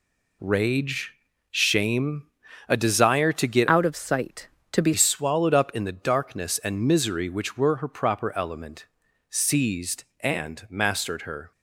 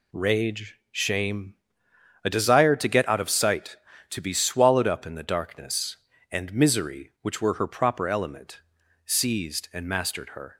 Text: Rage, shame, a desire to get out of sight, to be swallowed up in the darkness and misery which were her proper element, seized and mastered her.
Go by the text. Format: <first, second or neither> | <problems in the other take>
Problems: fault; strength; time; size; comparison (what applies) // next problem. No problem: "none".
second | changes voice from "out" to "be"; from 3.6 to 4.9 s; 1.3 s long